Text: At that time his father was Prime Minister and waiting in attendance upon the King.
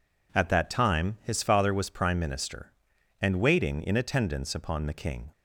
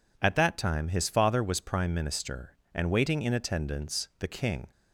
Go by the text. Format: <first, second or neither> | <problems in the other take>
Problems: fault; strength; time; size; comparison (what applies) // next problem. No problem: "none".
first | skips "upon"; at 4.1 s